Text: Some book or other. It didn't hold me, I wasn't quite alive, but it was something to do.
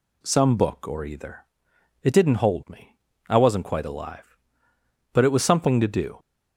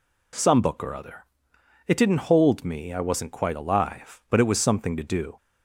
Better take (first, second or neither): second